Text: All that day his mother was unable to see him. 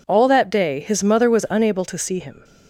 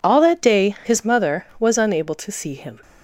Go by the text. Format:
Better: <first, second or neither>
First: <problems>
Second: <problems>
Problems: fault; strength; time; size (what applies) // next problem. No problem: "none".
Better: neither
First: none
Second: none